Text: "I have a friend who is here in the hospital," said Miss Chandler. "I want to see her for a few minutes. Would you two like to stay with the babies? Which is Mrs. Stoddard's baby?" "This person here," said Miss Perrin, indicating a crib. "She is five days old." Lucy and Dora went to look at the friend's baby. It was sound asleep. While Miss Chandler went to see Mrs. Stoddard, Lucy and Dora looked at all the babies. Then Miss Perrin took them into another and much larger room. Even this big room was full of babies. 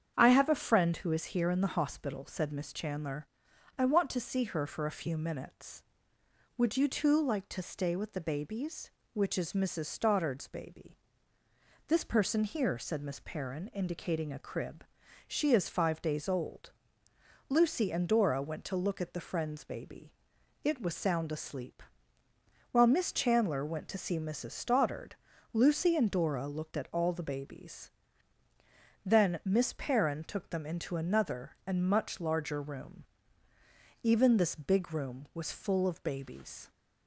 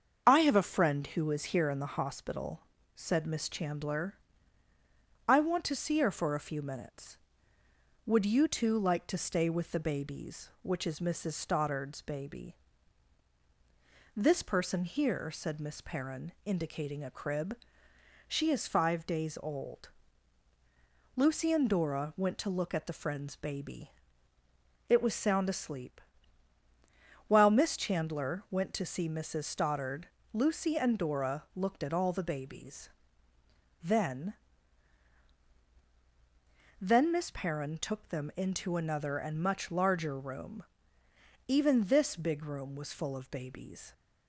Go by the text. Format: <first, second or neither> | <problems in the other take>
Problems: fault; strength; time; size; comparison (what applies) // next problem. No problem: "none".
first | starts louder than the rest; until 1.2 s; 7 dB; strong in the first // says "Then" twice; at 36.8 s